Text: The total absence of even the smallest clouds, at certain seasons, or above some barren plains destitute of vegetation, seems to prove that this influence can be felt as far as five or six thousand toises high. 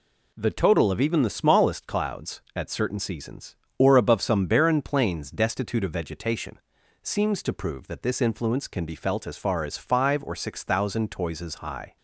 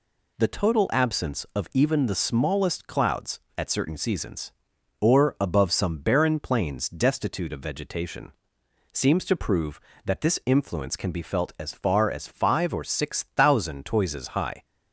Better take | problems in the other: second | skips "absence"; at 0.9 s

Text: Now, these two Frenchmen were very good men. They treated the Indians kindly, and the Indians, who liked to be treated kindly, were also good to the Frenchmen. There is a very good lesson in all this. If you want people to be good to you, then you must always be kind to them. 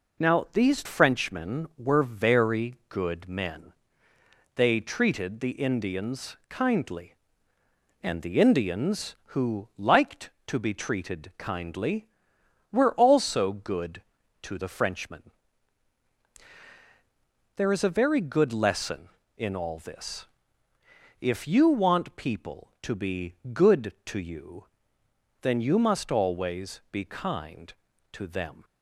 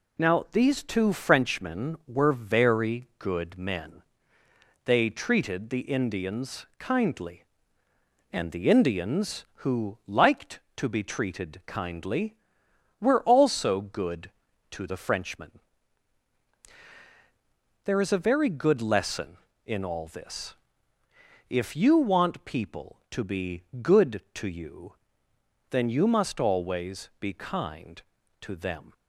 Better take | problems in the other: second | skips "two"; at 0.8 s // pauses between "be" and "good"; slight; at 23.3 s; 0.20 s long; slight in the second

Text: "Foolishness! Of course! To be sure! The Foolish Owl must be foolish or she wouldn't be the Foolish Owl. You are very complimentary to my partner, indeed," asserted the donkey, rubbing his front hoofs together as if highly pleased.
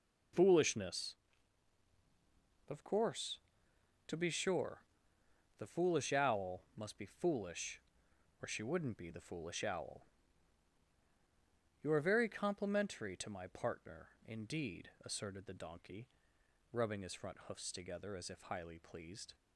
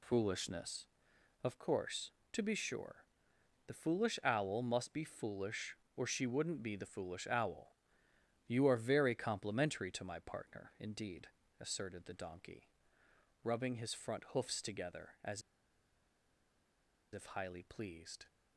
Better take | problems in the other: first | pauses between "as" and "if"; strong; at 15.4 s; 1.7 s long

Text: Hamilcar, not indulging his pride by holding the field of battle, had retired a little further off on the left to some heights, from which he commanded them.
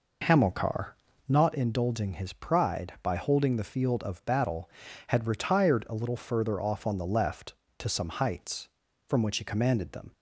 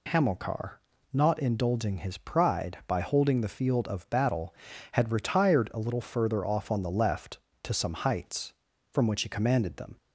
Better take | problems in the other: second | starts louder than the rest; noticeable; until 1.6 s; 4.5 dB

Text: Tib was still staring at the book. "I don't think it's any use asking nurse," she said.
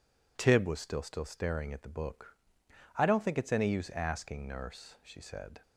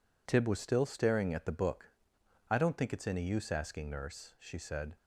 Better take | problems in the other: second | says "still" twice; at 1.0 s

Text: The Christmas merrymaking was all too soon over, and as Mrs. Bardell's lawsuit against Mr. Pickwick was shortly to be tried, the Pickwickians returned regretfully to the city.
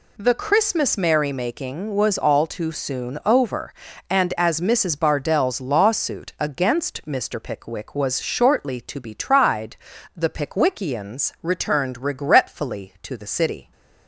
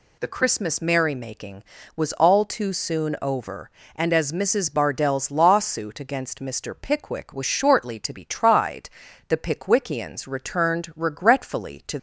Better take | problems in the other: first | stops before "the city"; at 11.9 s

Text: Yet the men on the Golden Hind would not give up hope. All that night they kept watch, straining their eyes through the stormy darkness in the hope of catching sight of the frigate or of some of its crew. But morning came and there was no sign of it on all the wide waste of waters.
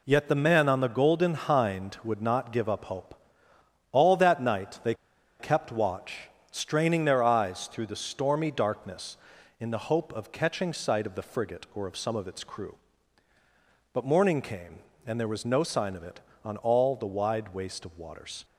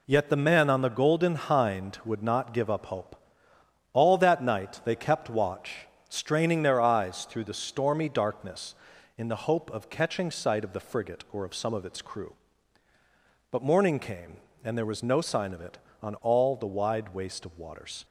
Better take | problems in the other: second | pauses between "they" and "kept"; noticeable; at 4.9 s; 0.46 s long

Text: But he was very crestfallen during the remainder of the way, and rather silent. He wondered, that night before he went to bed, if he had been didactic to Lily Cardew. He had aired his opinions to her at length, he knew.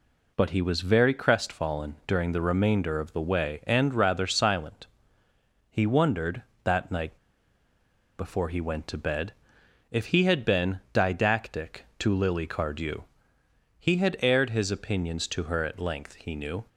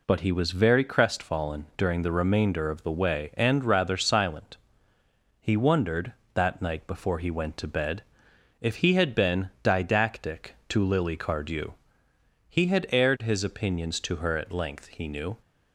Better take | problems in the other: second | pauses between "night" and "before"; at 7.1 s; 1.0 s long

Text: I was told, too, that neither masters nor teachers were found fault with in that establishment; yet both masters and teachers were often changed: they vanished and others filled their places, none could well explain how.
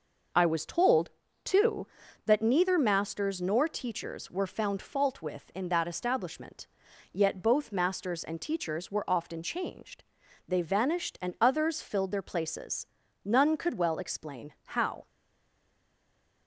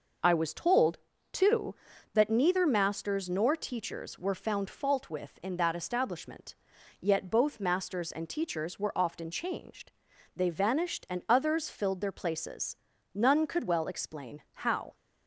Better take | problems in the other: second | stays silent after the last word; noticeable; from 15.0 s on; 1.4 s long

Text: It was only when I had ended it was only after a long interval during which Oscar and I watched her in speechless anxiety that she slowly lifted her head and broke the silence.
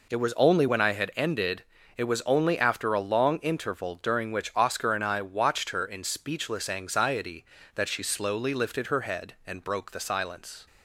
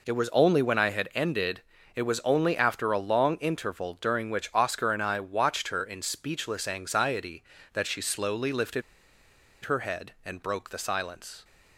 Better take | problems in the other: first | pauses between "ended" and "it"; slight; at 1.6 s; 0.34 s long; slight in the first // pauses between "lifted" and "her"; noticeable; at 8.8 s; 0.82 s long

